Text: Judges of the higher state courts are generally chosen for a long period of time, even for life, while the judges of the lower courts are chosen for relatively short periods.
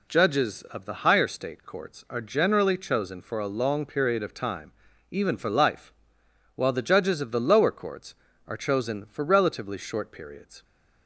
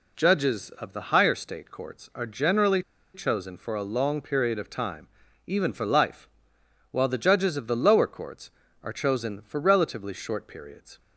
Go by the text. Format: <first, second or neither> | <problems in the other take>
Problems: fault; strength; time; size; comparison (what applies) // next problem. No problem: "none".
first | pauses between "generally" and "chosen"; slight; at 2.8 s; 0.33 s long